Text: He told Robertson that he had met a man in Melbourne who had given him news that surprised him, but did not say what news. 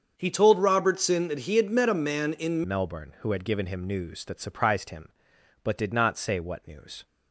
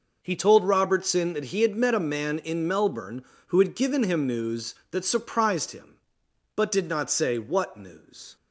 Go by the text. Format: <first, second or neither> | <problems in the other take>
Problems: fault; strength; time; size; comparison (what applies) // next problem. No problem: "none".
second | starts louder than the rest; strong; until 1.1 s; 7 dB // changes voice at "Melbourne"; from 2.6 s on; 4.4 s long